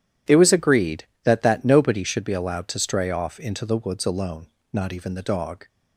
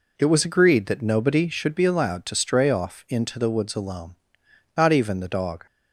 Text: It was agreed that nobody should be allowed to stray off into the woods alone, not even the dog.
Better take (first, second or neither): second